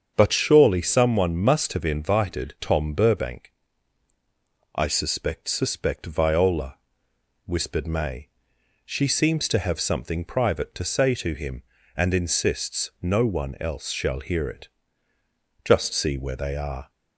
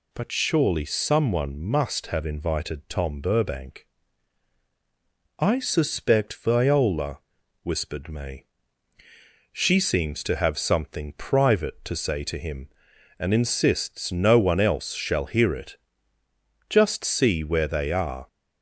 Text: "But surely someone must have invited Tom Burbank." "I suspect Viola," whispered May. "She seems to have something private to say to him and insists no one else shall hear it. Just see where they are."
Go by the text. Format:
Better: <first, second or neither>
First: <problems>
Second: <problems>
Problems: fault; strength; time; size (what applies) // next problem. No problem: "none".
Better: second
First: starts louder than the rest; strong; until 1.1 s; 7 dB // says "suspect" twice; at 5.4 s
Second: none